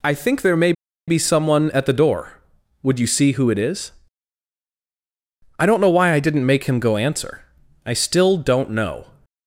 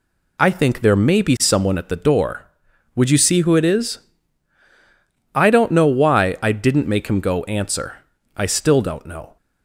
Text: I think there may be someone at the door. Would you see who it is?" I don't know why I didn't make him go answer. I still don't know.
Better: second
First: pauses between "may" and "be"; slight; at 0.7 s; 0.35 s long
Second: none

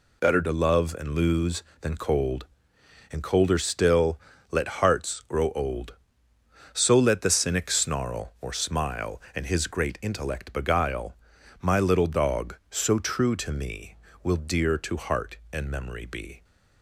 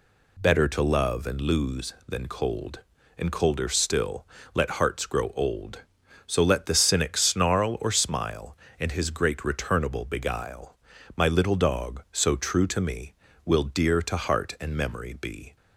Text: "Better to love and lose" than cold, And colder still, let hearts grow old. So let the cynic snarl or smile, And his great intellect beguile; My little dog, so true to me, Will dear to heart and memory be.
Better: first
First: none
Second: says "returnable" for "intellect"; at 9.4 s

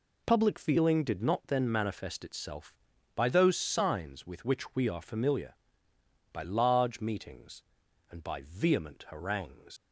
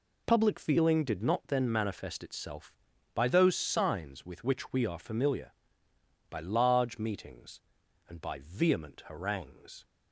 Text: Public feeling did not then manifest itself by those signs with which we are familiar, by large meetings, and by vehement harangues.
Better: second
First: leaves "harangues" unfinished; at 9.7 s; 100 ms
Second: none

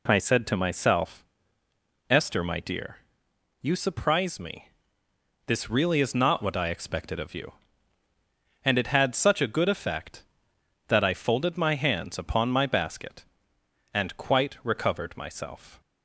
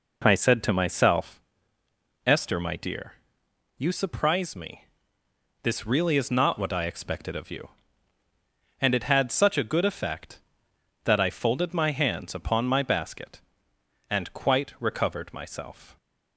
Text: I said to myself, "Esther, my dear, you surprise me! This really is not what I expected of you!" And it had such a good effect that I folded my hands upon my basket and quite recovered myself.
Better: first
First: none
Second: starts louder than the rest; noticeable; until 1.3 s; 4 dB

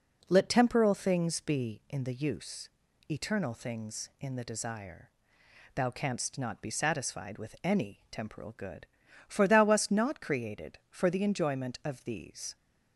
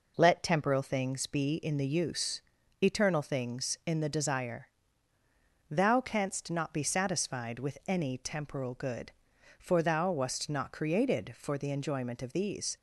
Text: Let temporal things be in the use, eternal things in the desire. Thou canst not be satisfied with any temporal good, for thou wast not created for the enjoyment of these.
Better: neither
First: none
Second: none

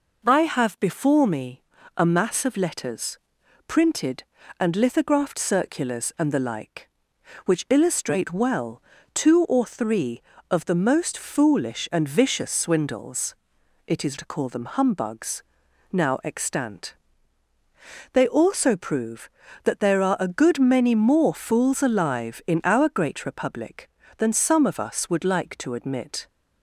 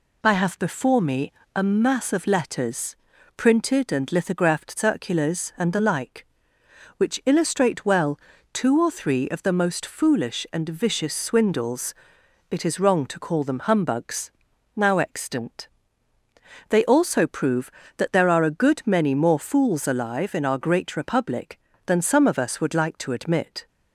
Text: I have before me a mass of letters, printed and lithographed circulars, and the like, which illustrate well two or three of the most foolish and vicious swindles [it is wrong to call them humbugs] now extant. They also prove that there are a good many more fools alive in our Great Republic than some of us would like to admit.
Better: second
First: pauses between "me" and "a"; slight; at 1.6 s; 0.32 s long // pauses between "well" and "two"; slight; at 8.8 s; 0.32 s long // pauses between "swindles" and "it"; noticeable; at 13.3 s; 0.52 s long // skips "wrong"; at 14.1 s // pauses between "humbugs" and "now"; noticeable; at 15.4 s; 0.48 s long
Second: pauses between "me" and "a"; slight; at 1.3 s; 0.24 s long // pauses between "well" and "two"; slight; at 8.1 s; 0.34 s long // pauses between "swindles" and "it"; noticeable; at 11.9 s; 0.56 s long // pauses between "humbugs" and "now"; at 14.3 s; 0.44 s long

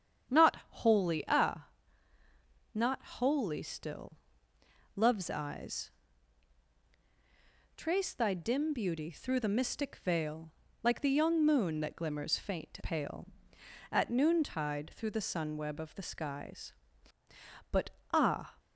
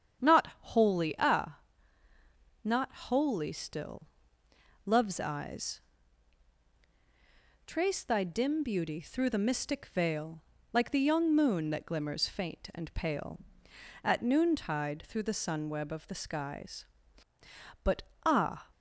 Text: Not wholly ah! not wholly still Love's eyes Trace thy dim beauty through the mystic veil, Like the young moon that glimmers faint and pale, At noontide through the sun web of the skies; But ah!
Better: second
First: starts louder than the rest; strong; until 1.4 s; 8.5 dB // pauses between "still" and "Love's"; noticeable; at 4.1 s; 0.78 s long // pauses between "eyes" and "Trace"; strong; at 5.8 s; 1.8 s long // skips "and"; at 12.8 s // pauses between "But" and "ah"; slight; at 17.8 s; 0.24 s long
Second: starts louder than the rest; strong; until 1.3 s; 8.5 dB // pauses between "still" and "Love's"; noticeable; at 4.0 s; 0.78 s long // pauses between "eyes" and "Trace"; strong; at 5.7 s; 1.8 s long // pauses between "But" and "ah"; slight; at 18.0 s; 0.24 s long

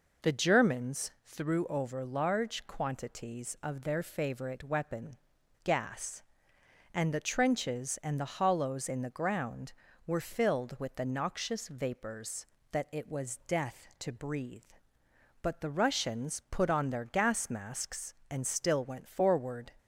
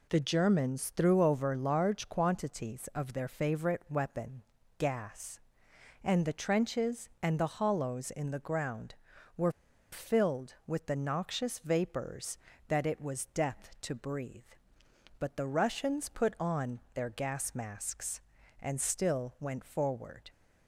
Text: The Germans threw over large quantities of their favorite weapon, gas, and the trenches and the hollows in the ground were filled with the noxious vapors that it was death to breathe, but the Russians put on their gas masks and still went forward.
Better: first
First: none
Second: pauses between "were" and "filled"; at 9.5 s; 0.40 s long

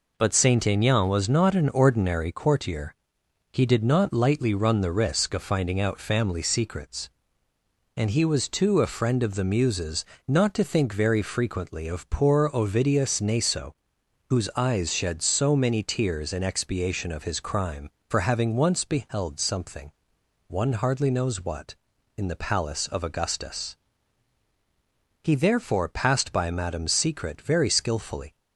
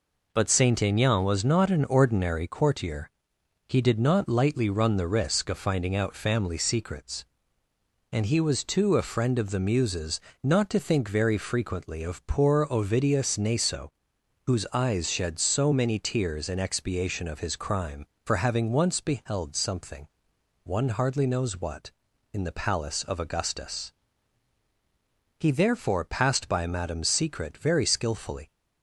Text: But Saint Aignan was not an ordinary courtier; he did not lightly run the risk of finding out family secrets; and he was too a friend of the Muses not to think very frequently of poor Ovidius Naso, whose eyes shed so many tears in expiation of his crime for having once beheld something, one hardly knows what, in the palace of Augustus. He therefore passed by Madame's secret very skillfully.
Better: neither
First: pauses between "Muses" and "not"; slight; at 10.0 s; 0.24 s long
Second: pauses between "Muses" and "not"; slight; at 10.1 s; 0.24 s long

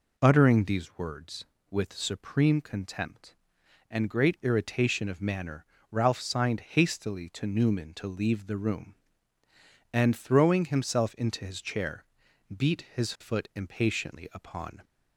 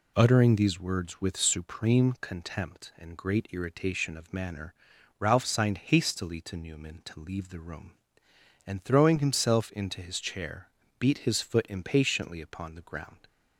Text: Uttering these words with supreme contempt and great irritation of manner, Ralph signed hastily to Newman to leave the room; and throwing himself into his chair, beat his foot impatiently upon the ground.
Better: second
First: stops before "the ground"; at 14.8 s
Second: none

